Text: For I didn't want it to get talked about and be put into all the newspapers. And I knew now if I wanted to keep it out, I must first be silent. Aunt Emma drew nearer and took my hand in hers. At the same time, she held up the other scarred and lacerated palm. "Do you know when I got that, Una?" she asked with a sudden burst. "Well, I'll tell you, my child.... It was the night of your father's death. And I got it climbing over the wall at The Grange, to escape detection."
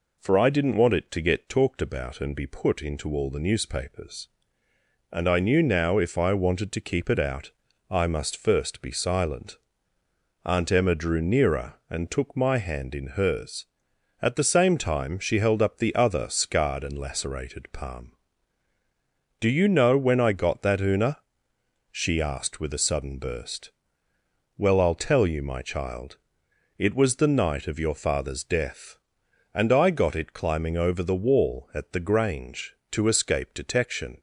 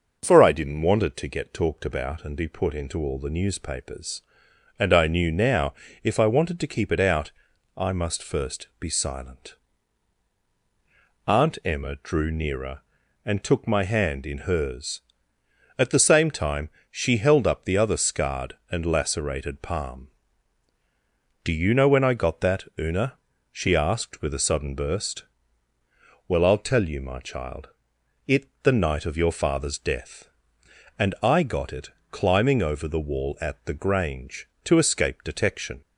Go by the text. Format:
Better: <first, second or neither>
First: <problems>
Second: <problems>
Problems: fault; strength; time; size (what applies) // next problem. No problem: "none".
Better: first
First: none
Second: pauses between "now" and "if"; slight; at 5.7 s; 0.30 s long // skips "was"; at 28.5 s // pauses between "it" and "climbing"; slight; at 31.8 s; 0.22 s long